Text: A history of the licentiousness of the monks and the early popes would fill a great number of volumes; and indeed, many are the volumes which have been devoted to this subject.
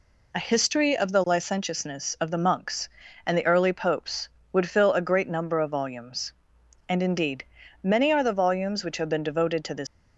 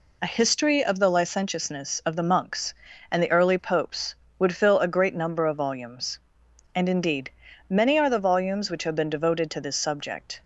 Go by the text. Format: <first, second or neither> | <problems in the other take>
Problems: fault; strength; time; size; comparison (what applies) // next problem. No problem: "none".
second | stops before "subject"; at 9.8 s